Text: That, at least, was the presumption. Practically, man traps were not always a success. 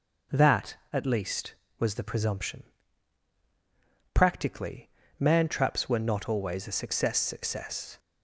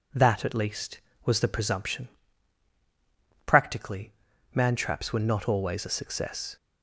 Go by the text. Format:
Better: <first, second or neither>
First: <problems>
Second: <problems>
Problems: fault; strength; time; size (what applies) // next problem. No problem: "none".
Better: second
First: says "success" twice; at 7.1 s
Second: none